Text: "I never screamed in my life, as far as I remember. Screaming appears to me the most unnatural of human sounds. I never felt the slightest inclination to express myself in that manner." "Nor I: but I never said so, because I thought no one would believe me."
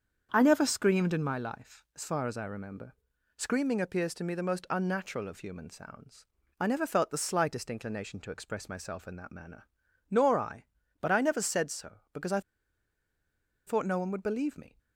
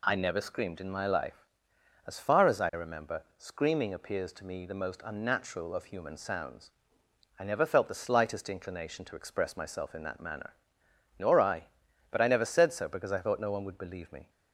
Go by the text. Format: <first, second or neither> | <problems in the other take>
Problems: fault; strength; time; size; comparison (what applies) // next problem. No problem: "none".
second | starts louder than the rest; strong; until 1.3 s; 7 dB // pauses between "I" and "thought"; strong; at 12.3 s; 1.2 s long